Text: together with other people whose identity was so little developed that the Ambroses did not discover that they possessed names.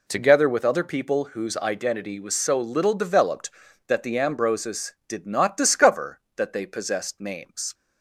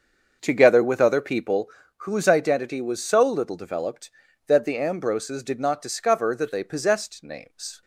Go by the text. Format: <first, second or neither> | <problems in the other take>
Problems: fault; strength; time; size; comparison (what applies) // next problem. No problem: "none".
first | starts louder than the rest; until 1.6 s; 6.5 dB // pauses between "people" and "whose"; slight; at 1.6 s; 0.30 s long